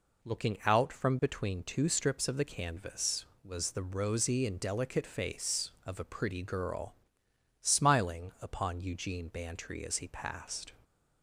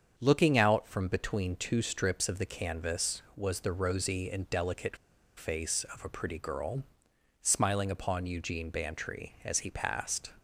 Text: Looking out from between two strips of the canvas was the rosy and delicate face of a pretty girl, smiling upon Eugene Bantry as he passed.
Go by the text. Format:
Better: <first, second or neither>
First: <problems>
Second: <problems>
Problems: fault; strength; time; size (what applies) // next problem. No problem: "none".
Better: first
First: none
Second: starts louder than the rest; strong; until 1.1 s; 7 dB // pauses between "delicate" and "face"; at 4.9 s; 0.40 s long